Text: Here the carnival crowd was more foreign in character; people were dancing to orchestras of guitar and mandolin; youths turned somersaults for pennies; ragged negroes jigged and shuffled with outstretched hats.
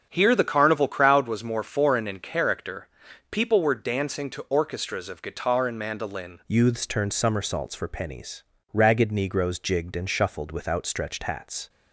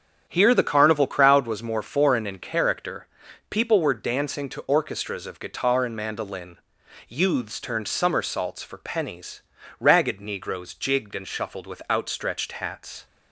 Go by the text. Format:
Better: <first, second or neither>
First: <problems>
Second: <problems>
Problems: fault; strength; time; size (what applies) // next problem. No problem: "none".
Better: second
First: starts louder than the rest; strong; until 1.1 s; 7.5 dB // changes voice at "youths"; from 6.4 s on; 5.2 s long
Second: starts louder than the rest; strong; until 1.3 s; 8.5 dB